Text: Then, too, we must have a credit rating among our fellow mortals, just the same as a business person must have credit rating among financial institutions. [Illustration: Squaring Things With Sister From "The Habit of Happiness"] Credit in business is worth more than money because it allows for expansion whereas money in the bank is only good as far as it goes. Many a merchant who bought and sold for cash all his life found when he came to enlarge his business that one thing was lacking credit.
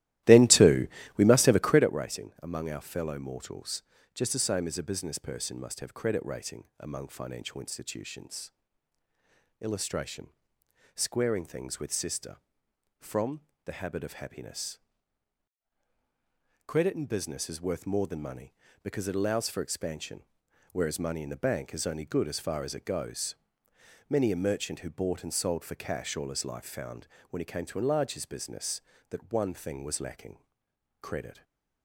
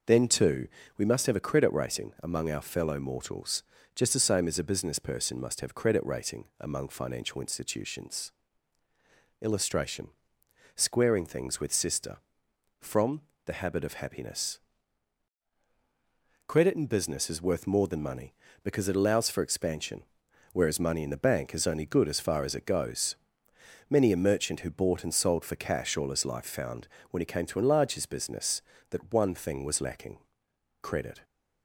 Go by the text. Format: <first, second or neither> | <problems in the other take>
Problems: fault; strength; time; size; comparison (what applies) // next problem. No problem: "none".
second | starts louder than the rest; strong; until 1.9 s; 15.5 dB // pauses between "From" and "The"; slight; at 13.4 s; 0.24 s long; slight in the second // pauses between "Happiness" and "Credit"; strong; at 14.7 s; 1.8 s long; strong in the second // pauses between "expansion" and "whereas"; noticeable; at 20.2 s; 0.48 s long; noticeable in the second // pauses between "found" and "when"; slight; at 27.0 s; 0.24 s long; slight in the second // pauses between "lacking" and "credit"; noticeable; at 30.3 s; 0.62 s long; noticeable in the second // stays silent after the last word; slight; from 31.3 s on; 0.5 s long